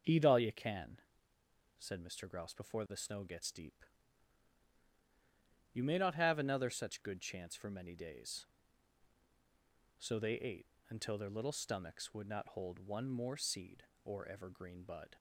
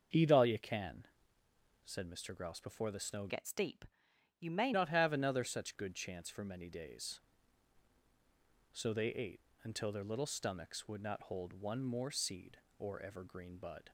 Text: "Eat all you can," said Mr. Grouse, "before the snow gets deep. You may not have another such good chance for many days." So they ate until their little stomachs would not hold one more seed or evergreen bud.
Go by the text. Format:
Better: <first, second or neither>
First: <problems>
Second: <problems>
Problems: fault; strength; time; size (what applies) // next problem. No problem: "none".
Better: first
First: starts louder than the rest; until 1.8 s; 6.5 dB // pauses between "ate" and "until"; slight; at 10.6 s; 0.22 s long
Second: starts louder than the rest; until 1.9 s; 6 dB // changes voice from "gets" to "may"; from 3.2 to 4.7 s; 1.5 s long // pauses between "ate" and "until"; slight; at 9.4 s; 0.22 s long